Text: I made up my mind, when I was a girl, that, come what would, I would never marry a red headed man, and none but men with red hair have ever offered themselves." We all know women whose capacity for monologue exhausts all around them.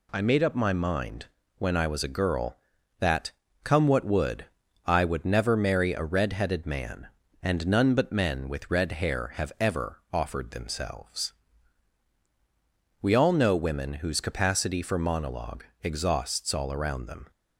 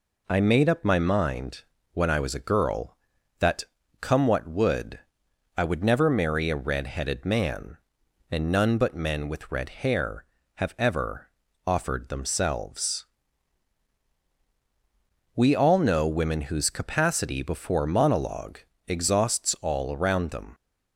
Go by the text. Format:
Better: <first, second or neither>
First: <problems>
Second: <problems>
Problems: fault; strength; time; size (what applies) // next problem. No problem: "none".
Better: first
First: pauses between "monologue" and "exhausts"; slight; at 15.6 s; 0.18 s long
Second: pauses between "ever" and "offered"; at 11.2 s; 0.38 s long // says "before" for "for"; at 17.4 s // pauses between "monologue" and "exhausts"; slight; at 18.5 s; 0.28 s long